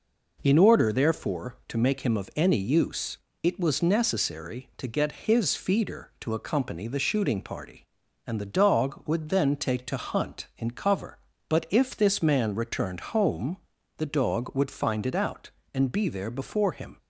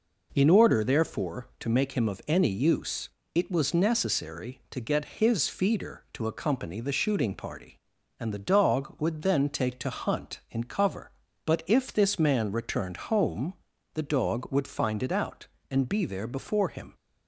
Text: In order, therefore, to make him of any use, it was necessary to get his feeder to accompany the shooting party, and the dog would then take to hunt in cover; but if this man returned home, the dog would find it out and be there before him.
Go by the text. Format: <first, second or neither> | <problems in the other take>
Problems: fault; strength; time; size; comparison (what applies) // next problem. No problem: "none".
neither | none